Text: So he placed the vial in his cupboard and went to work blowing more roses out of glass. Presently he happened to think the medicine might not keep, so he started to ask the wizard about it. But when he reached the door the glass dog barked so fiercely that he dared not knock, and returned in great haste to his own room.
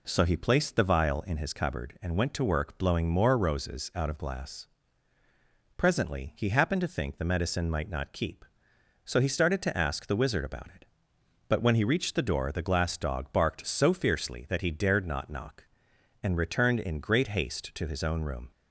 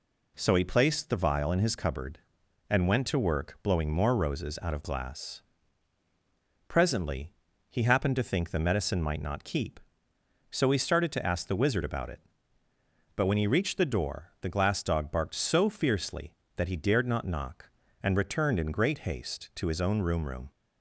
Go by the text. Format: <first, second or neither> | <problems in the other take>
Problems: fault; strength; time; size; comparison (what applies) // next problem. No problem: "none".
first | pauses between "Presently" and "he"; at 7.3 s; 0.38 s long // says "room" twice; at 20.2 s